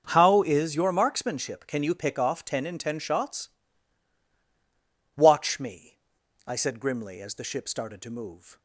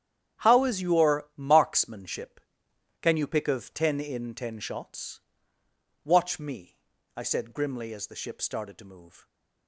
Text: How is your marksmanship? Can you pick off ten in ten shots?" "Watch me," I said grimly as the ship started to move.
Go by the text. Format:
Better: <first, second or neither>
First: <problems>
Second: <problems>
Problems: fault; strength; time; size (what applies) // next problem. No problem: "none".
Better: first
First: starts louder than the rest; until 1.1 s; 6.5 dB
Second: starts louder than the rest; strong; until 1.5 s; 9 dB // says "of" for "off"; at 3.4 s